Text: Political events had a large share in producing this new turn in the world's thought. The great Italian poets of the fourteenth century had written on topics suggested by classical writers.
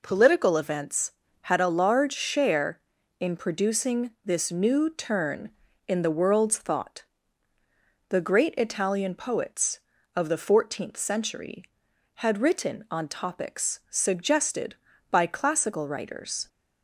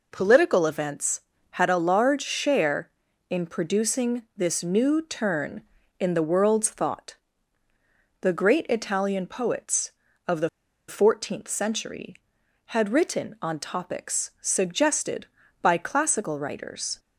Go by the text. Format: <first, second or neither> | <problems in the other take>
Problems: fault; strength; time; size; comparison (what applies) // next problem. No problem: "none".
first | pauses between "the" and "fourteenth"; at 10.4 s; 0.39 s long